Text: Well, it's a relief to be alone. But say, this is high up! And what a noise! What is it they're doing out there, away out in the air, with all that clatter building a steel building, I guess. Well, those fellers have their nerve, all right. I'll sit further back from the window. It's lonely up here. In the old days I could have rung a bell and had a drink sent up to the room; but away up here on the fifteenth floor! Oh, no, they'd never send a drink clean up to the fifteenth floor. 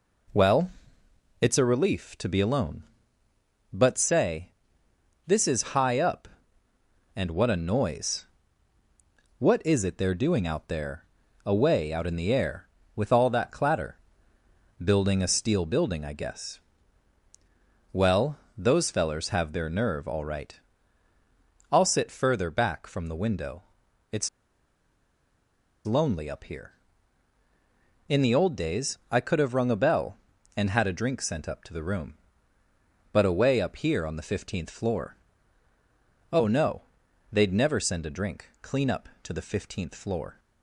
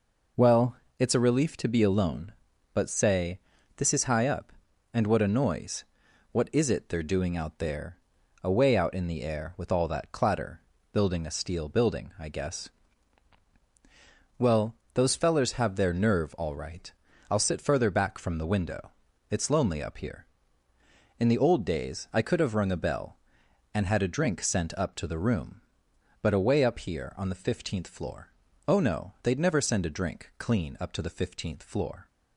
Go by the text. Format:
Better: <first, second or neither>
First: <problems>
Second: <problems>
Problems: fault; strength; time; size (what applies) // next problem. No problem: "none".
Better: second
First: pauses between "clatter" and "building"; noticeable; at 13.9 s; 0.86 s long // pauses between "It's" and "lonely"; strong; at 24.2 s; 1.5 s long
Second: pauses between "clatter" and "building"; slight; at 10.5 s; 0.32 s long